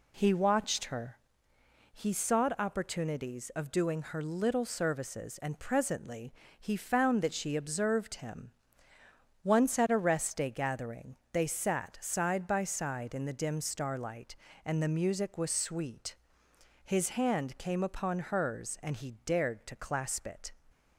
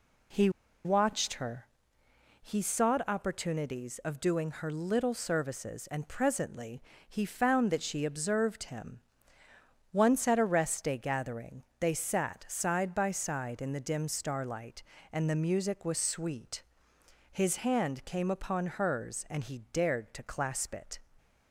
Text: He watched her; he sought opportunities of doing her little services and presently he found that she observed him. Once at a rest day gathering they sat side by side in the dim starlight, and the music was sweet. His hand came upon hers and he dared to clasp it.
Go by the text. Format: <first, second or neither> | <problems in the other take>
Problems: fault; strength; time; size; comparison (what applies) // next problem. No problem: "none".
first | pauses between "He" and "watched"; slight; at 0.4 s; 0.35 s long // pauses between "presently" and "he"; slight; at 6.8 s; 0.24 s long; slight in the first // pauses between "gathering" and "they"; slight; at 11.6 s; 0.16 s long; slight in the first